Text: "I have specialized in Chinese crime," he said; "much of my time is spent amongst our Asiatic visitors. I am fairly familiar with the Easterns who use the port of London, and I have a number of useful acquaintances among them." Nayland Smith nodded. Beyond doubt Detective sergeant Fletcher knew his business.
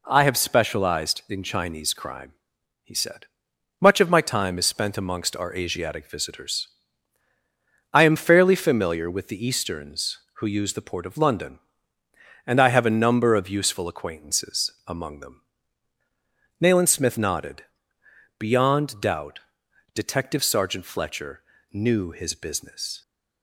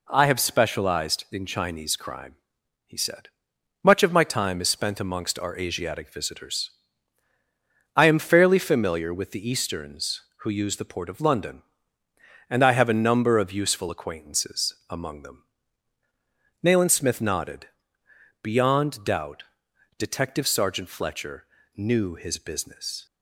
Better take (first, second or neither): neither